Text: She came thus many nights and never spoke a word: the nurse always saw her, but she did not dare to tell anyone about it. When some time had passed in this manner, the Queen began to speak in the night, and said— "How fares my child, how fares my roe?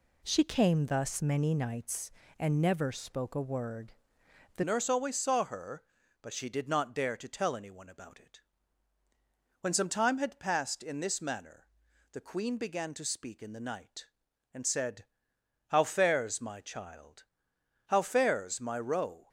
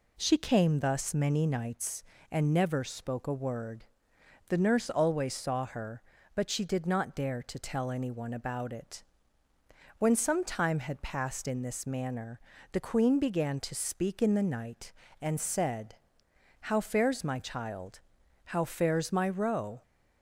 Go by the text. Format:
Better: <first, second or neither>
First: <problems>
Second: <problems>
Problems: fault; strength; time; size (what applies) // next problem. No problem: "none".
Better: second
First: changes voice at "nurse"; from 4.6 s on; 14.6 s long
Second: none